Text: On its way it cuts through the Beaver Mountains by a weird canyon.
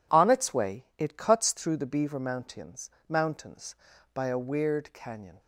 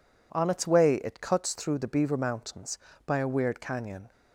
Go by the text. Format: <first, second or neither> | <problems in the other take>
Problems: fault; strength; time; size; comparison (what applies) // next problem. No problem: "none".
second | says "Mountains" twice; at 3.0 s